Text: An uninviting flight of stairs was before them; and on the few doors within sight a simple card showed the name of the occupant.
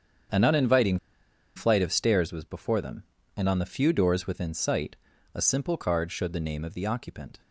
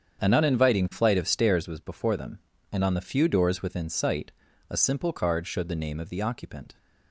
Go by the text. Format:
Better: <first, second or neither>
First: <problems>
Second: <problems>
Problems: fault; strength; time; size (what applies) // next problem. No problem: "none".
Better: second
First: starts louder than the rest; strong; until 1.9 s; 7.5 dB // pauses between "uninviting" and "flight"; noticeable; at 0.9 s; 0.59 s long // pauses between "sight" and "a"; at 4.9 s; 0.38 s long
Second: starts louder than the rest; strong; until 1.2 s; 7.5 dB // pauses between "sight" and "a"; at 4.3 s; 0.38 s long